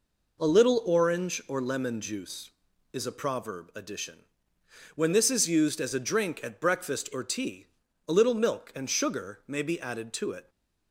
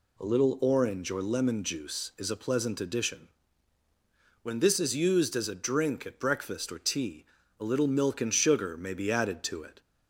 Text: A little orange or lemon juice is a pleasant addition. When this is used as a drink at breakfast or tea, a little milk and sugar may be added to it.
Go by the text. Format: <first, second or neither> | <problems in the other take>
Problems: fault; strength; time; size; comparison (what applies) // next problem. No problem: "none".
second | says "proverb" for "pleasant"; at 3.1 s